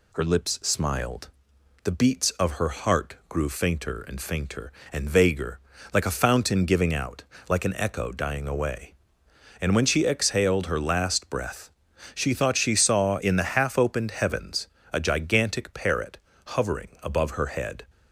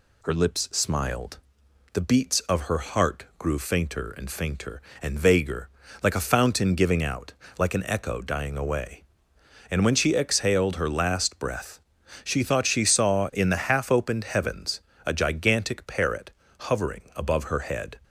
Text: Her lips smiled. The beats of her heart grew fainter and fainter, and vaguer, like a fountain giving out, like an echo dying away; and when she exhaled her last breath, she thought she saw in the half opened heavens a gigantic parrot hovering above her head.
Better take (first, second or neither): neither